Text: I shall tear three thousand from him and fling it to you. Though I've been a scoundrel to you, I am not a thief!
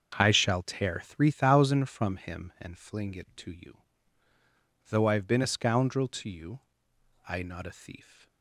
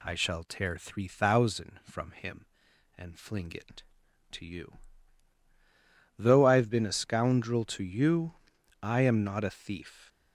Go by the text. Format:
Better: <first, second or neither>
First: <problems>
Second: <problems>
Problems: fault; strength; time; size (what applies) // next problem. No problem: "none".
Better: second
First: starts louder than the rest; until 1.2 s; 6.5 dB // skips "am"; at 7.4 s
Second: none